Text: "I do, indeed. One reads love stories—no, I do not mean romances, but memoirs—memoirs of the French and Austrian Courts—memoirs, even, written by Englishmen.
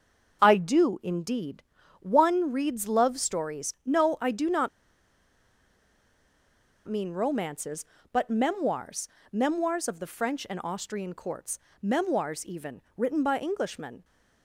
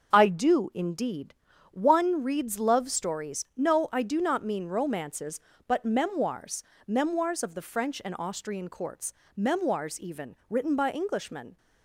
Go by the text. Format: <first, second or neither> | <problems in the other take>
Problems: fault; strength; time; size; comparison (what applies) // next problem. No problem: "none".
second | starts louder than the rest; until 1.4 s; 6 dB // pauses between "not" and "mean"; strong; at 4.6 s; 2.1 s long